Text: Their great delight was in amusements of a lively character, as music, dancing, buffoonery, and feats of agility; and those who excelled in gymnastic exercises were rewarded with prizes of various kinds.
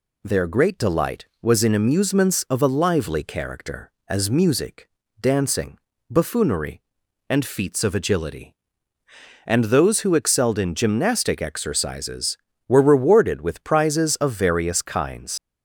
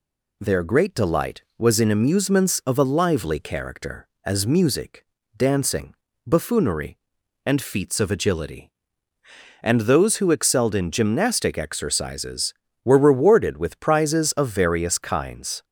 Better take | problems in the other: second | leaves "kinds" unfinished; at 15.3 s; 100 ms

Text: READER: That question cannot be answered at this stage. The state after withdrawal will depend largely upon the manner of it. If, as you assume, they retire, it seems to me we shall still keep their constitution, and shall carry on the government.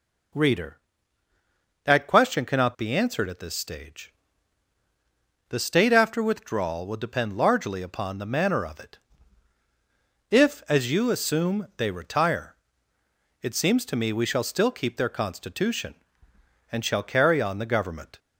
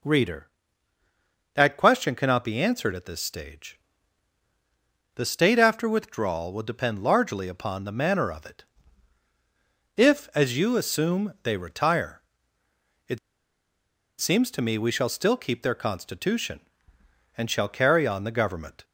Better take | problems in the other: first | pauses between "it" and "seems"; at 13.1 s; 1.0 s long

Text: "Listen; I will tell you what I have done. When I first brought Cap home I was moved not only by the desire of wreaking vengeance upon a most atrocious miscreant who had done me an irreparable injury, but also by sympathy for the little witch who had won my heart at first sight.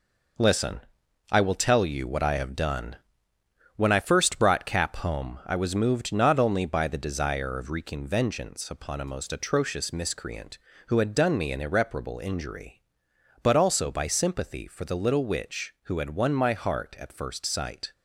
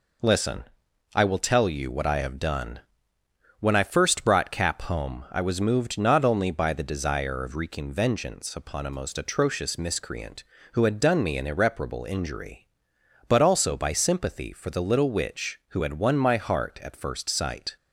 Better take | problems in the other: second | gets quieter; strong; throughout; 7.5 dB

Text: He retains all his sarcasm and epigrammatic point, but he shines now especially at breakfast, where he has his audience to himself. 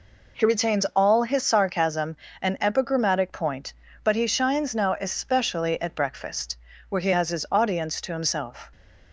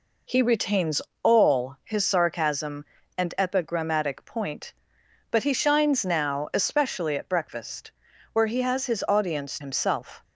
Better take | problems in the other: first | pauses between "retains" and "all"; slight; at 1.0 s; 0.22 s long // skips "to"; at 9.6 s

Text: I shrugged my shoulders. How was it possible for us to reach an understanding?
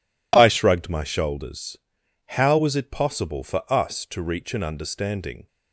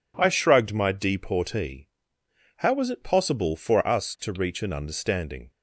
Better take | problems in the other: first | says "deportee" for "shoulders"; at 0.9 s

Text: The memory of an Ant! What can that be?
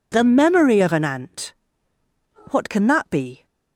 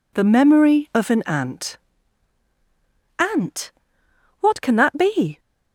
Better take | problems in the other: first | says "Ant" twice; at 3.1 s

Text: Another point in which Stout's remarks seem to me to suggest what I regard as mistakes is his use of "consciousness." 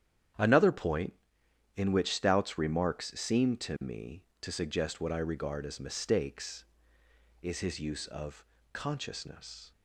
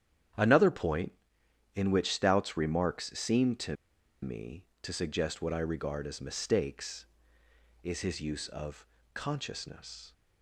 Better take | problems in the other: first | starts louder than the rest; strong; until 1.9 s; 9.5 dB; strong in the first // pauses between "to" and "me"; noticeable; at 3.7 s; 0.47 s long // pauses between "of" and "consciousness"; slight; at 8.8 s; 0.28 s long; slight in the first

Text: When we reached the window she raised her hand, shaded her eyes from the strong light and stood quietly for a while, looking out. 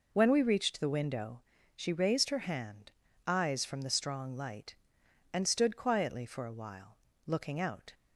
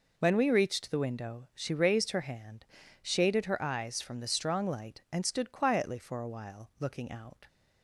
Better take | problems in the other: second | pauses between "window" and "she"; slight; at 1.4 s; 0.36 s long // skips "shaded her"; at 3.0 s

